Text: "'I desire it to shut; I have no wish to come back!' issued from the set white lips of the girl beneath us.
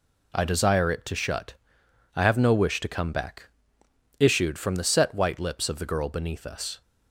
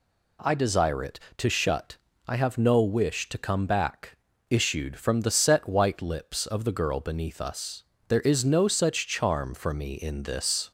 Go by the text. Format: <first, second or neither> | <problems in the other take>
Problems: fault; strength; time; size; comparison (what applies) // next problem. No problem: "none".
first | goes on to say "There is no such charm for me in this"; strong; from 8.0 s on; 2.6 s long